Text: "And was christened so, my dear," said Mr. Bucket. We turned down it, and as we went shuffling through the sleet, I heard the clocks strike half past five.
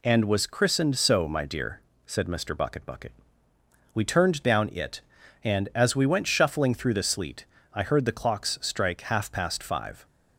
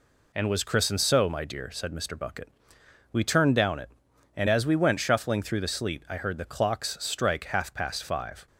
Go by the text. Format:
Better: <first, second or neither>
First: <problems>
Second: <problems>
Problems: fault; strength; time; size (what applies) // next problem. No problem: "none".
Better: second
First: says "Bucket" twice; at 2.8 s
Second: none